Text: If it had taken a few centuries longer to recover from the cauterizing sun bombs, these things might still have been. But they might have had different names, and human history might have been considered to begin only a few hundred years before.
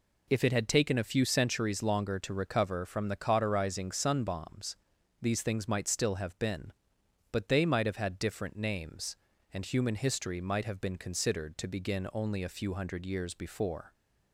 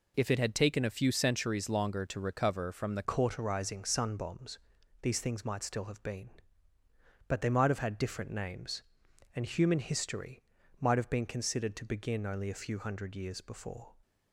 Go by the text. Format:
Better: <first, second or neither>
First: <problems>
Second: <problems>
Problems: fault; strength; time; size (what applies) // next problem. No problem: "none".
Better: first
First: none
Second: changes voice at "cauterizing"; from 3.0 s on; 10.9 s long // pauses between "history" and "might"; at 10.4 s; 0.38 s long